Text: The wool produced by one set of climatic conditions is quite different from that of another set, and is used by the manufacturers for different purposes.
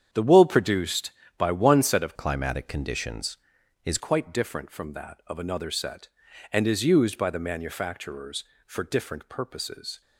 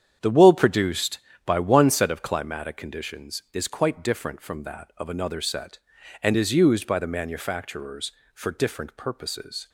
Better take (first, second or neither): second